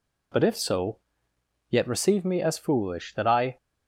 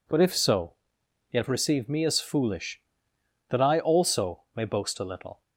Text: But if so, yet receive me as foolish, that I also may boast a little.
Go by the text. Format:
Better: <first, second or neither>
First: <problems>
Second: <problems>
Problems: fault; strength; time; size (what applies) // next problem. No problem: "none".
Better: second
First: stops before "also may boast a little"; at 3.5 s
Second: none